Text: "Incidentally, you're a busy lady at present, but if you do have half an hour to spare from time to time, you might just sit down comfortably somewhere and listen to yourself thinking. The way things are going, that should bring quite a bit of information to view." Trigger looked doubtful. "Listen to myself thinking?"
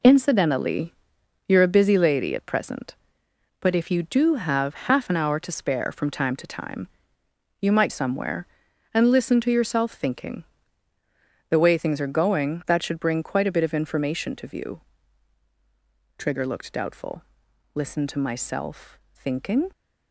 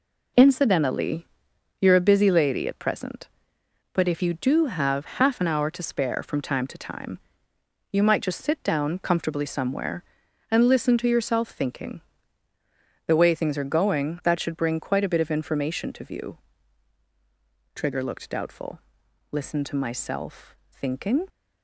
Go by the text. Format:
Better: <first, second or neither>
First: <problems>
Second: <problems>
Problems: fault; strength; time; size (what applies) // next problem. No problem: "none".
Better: second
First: skips "just sit down comfortably"; at 7.9 s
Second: none